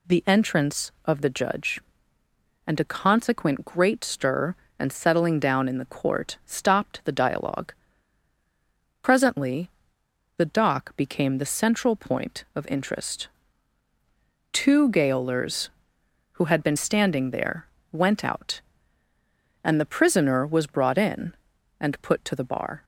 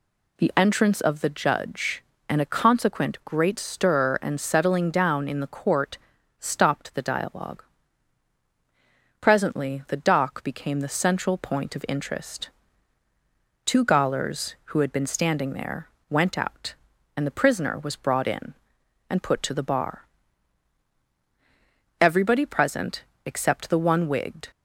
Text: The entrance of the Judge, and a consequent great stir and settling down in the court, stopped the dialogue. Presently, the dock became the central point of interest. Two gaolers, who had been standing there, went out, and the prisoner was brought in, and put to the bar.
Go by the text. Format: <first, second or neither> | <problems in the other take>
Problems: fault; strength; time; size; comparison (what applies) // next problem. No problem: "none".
first | goes on to say "Everybody present except the one wigged"; strong; from 21.9 s on; 2.5 s long